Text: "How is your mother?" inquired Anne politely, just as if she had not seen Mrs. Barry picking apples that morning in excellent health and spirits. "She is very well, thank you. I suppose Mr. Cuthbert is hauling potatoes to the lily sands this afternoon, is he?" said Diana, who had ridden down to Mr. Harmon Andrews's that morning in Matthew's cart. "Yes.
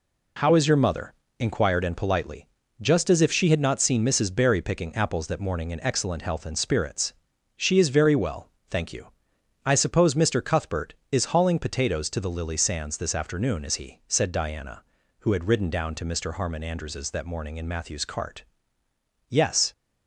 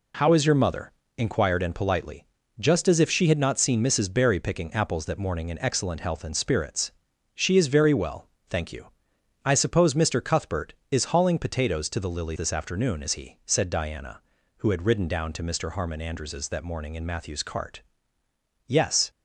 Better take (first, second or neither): first